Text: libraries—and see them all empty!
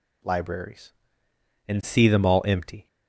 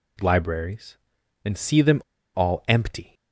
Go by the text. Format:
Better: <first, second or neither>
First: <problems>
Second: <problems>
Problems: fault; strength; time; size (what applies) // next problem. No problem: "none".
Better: first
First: none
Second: pauses between "them" and "all"; slight; at 2.0 s; 0.34 s long